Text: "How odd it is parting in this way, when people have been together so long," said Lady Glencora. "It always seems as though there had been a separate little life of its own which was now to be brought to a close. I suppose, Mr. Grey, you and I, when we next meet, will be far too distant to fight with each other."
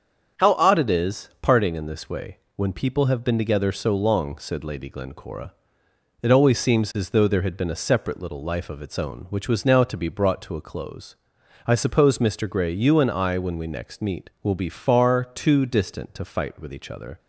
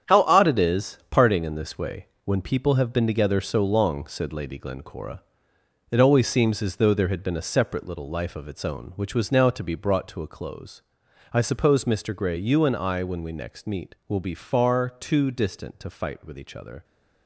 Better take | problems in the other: first | gets quieter; strong; throughout; 9 dB // starts louder than the rest; strong; until 1.1 s; 8.5 dB; strong in the first

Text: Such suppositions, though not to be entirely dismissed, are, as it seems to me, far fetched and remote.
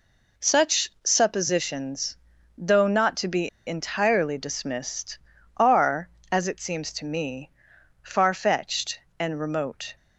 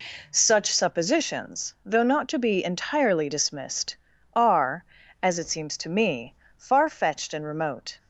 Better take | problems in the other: second | pauses between "be" and "entirely"; slight; at 3.4 s; 0.18 s long

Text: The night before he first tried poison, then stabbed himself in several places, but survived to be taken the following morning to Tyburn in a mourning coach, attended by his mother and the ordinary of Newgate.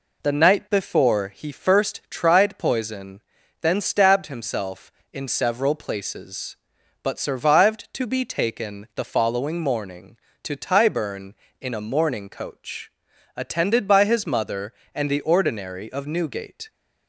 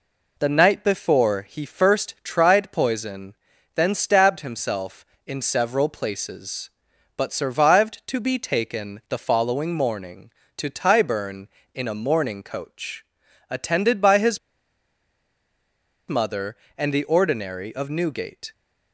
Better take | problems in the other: first | pauses between "his" and "mother"; strong; at 14.3 s; 1.6 s long

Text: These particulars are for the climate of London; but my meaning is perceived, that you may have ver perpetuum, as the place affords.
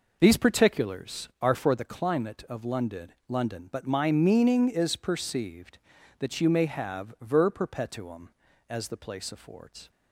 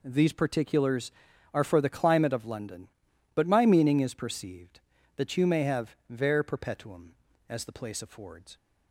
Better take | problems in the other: second | says "London" twice; at 3.2 s

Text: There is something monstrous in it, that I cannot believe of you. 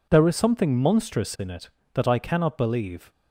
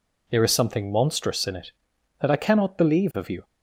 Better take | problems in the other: second | stops before "of you"; at 3.1 s

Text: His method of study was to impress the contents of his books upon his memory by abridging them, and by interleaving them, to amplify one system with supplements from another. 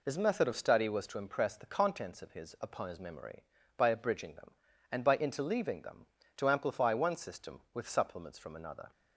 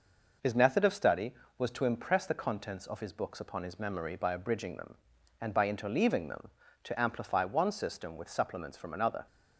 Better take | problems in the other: second | skips "books"; at 2.5 s

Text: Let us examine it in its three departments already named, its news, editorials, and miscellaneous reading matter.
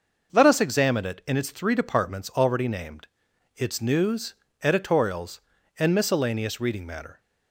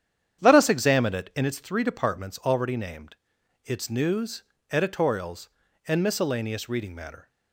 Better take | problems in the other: first | starts louder than the rest; strong; until 1.5 s; 9 dB

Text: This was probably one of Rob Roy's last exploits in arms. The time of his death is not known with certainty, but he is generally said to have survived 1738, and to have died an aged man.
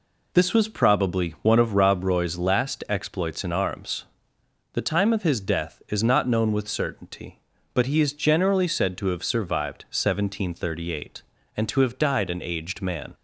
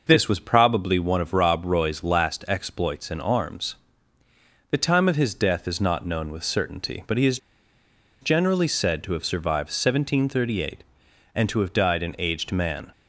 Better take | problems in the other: first | pauses between "is" and "generally"; noticeable; at 7.3 s; 0.83 s long

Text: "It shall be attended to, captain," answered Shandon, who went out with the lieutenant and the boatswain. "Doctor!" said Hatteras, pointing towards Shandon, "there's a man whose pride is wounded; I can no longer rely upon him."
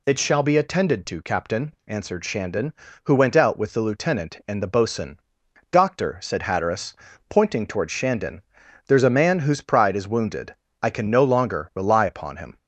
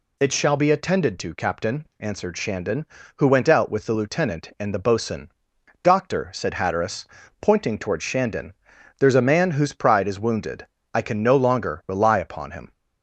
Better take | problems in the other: neither | none

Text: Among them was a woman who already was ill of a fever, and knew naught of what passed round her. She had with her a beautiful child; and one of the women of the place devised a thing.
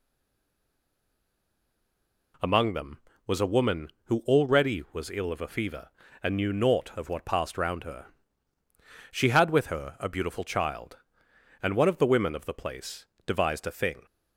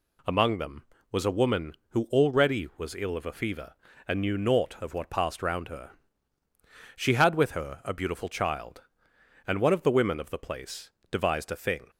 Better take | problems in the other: second | stays silent before the first word; until 2.3 s; 2.3 s long // pauses between "place" and "devised"; slight; at 13.0 s; 0.20 s long; slight in the second

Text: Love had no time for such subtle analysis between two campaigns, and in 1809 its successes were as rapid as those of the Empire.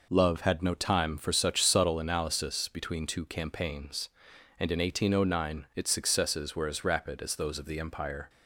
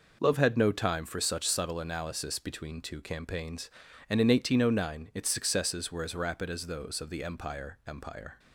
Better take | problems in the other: first | says "Empire" twice; at 7.8 s

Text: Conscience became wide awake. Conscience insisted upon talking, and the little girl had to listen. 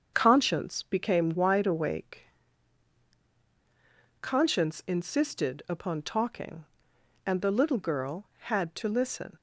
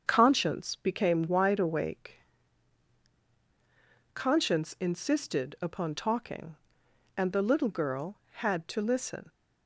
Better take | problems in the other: neither | starts louder than the rest; the same in both

